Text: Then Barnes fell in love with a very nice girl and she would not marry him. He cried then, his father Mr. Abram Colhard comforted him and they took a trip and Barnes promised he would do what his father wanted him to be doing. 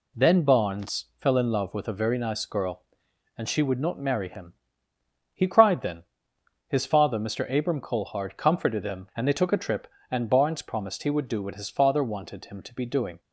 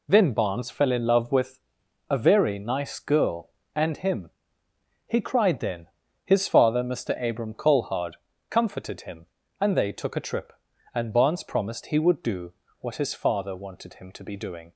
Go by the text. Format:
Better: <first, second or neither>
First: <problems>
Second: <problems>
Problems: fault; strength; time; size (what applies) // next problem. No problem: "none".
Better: first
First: none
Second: pauses between "with" and "a"; noticeable; at 1.5 s; 0.50 s long // skips "she would not marry"; at 3.9 s // pauses between "Colhard" and "comforted"; slight; at 8.1 s; 0.36 s long // pauses between "do" and "what"; slight; at 12.5 s; 0.28 s long